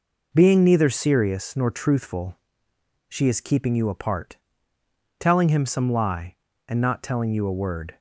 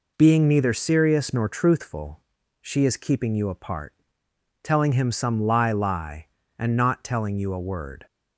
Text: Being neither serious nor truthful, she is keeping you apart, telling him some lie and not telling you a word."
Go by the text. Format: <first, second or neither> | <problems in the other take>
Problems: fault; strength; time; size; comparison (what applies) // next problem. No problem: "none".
first | says "lie" twice; at 5.7 s